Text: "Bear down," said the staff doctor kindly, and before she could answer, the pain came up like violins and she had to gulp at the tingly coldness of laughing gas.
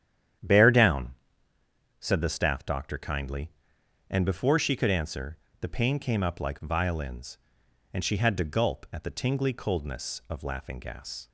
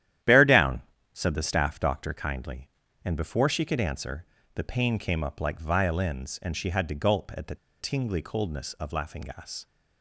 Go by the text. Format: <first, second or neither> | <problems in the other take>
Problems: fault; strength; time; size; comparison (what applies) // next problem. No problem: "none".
first | starts louder than the rest; strong; until 1.5 s; 11.5 dB; strong in the first // pauses between "the" and "tingly"; slight; at 7.5 s; 0.24 s long